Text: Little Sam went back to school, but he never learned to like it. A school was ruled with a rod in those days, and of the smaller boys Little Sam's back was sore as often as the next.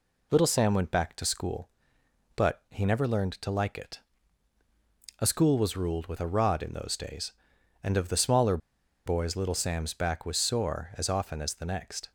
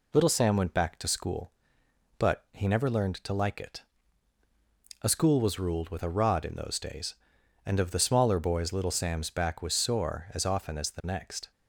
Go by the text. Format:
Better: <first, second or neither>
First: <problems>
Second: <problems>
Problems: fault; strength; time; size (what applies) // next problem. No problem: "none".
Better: second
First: pauses between "smaller" and "boys"; noticeable; at 8.5 s; 0.49 s long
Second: none